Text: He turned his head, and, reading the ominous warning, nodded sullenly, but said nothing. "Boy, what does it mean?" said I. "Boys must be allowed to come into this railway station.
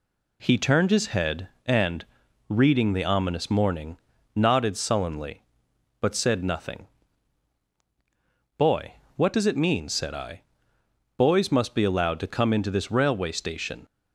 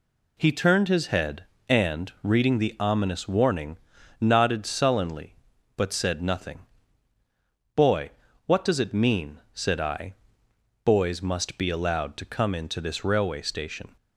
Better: second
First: says "morning" for "warning"; at 3.5 s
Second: none

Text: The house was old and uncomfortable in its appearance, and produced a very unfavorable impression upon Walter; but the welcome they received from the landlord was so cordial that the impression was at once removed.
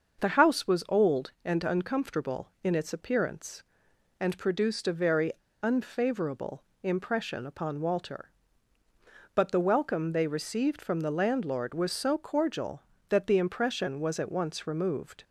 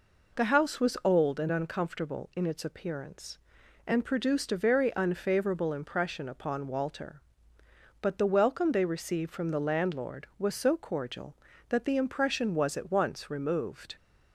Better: second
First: starts louder than the rest; until 1.2 s; 6.5 dB // pauses between "very" and "unfavorable"; slight; at 5.3 s; 0.31 s long // pauses between "unfavorable" and "impression"; slight; at 6.6 s; 0.20 s long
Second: none

